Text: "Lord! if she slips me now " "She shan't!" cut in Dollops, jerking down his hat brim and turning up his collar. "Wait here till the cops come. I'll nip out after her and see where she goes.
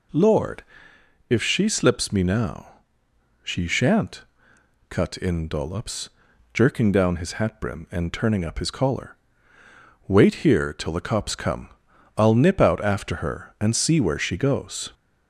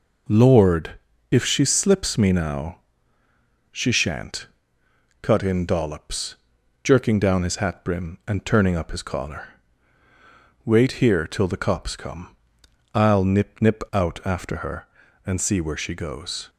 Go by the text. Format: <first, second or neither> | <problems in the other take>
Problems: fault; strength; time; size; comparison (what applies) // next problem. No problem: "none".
first | says "nip" twice; at 13.6 s